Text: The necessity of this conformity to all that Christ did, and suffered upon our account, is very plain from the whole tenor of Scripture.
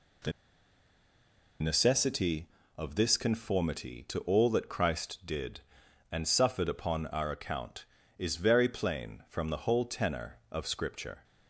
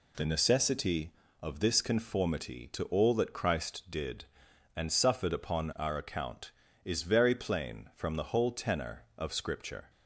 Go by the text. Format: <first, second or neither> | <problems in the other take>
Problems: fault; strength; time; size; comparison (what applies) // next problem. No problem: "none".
second | pauses between "The" and "necessity"; strong; at 0.3 s; 1.2 s long